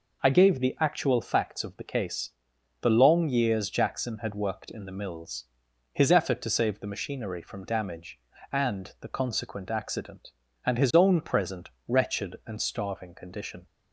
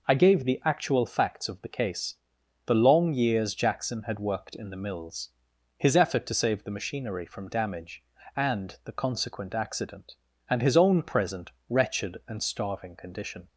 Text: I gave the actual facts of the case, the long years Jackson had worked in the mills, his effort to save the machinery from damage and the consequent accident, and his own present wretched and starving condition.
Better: neither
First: pauses between "present" and "wretched"; slight; at 11.6 s; 0.18 s long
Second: pauses between "present" and "wretched"; slight; at 11.5 s; 0.18 s long

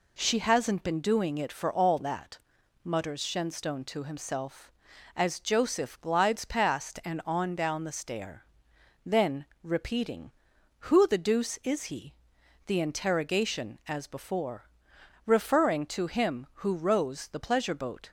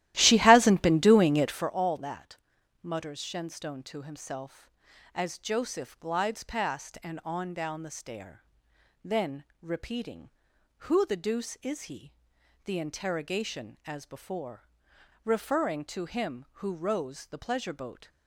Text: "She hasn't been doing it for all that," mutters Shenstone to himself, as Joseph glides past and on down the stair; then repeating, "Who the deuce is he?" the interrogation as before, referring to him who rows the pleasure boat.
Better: first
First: pauses between "then" and "repeating"; slight; at 9.4 s; 0.16 s long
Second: starts louder than the rest; strong; until 1.7 s; 14.5 dB // pauses between "then" and "repeating"; slight; at 9.4 s; 0.16 s long

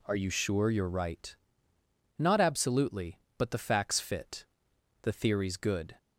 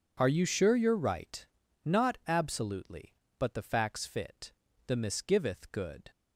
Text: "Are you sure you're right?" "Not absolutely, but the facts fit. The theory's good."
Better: first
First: none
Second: says "misgiveth" for "theory's"; at 4.9 s

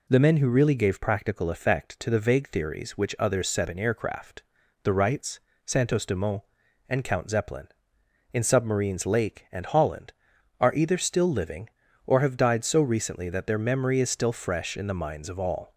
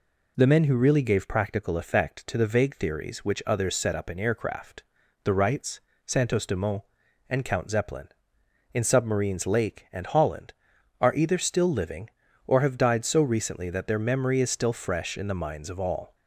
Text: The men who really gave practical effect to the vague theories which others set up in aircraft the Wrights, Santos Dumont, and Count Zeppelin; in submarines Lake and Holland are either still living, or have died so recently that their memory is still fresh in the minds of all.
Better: second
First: skips "up"; at 3.6 s // pauses between "aircraft" and "the"; at 4.4 s; 0.42 s long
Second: pauses between "aircraft" and "the"; at 4.8 s; 0.42 s long

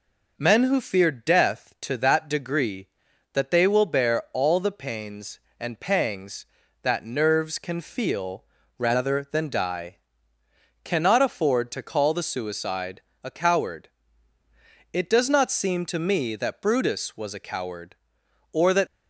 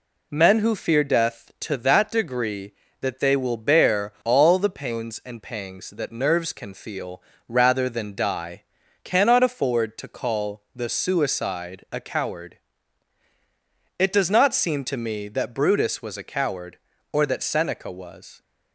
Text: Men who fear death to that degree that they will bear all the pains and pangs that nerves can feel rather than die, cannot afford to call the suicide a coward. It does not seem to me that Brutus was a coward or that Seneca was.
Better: second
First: pauses between "feel" and "rather"; slight; at 8.4 s; 0.34 s long // pauses between "suicide" and "a"; slight; at 13.0 s; 0.22 s long // stops before "Seneca was"; at 18.8 s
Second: pauses between "feel" and "rather"; slight; at 7.1 s; 0.28 s long

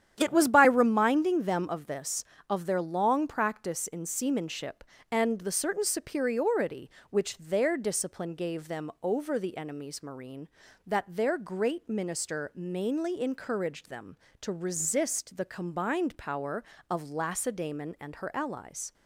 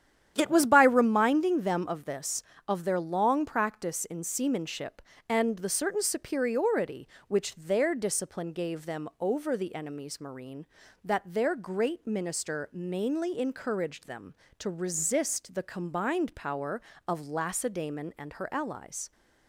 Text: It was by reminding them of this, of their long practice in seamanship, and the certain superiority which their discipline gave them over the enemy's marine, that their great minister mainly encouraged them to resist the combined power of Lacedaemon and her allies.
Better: neither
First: starts louder than the rest; strong; until 1.1 s; 10 dB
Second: starts louder than the rest; strong; until 1.3 s; 10 dB

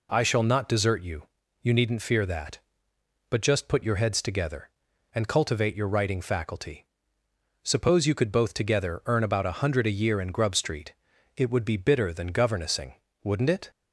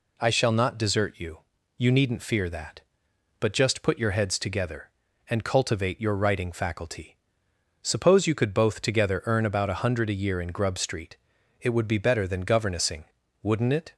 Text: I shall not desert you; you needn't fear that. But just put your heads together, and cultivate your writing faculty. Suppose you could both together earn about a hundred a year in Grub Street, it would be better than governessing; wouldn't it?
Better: second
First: says "bitter" for "better"; at 11.7 s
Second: none

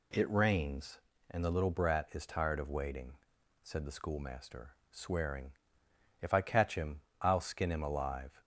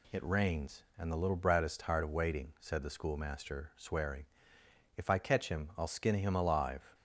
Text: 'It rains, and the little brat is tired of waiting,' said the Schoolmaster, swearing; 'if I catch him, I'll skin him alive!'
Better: neither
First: none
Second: none

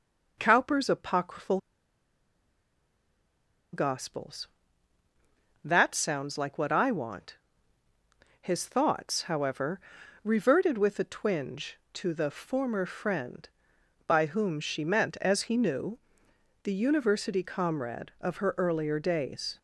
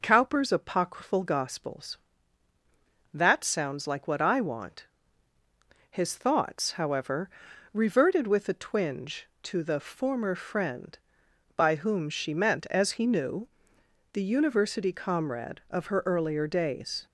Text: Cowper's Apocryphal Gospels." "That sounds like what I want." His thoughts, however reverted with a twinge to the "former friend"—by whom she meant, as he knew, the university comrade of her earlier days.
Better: second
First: pauses between "Apocryphal" and "Gospels"; strong; at 1.5 s; 2.1 s long // pauses between "however" and "reverted"; at 9.7 s; 0.44 s long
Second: pauses between "however" and "reverted"; at 7.2 s; 0.44 s long

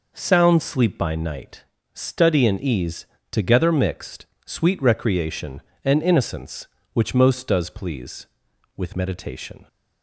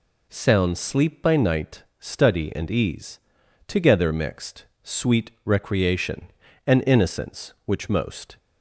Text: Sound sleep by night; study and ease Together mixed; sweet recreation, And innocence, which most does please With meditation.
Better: first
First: pauses between "ease" and "Together"; slight; at 3.0 s; 0.24 s long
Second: pauses between "ease" and "Together"; noticeable; at 3.1 s; 0.48 s long // stops before "does please With meditation"; at 8.3 s

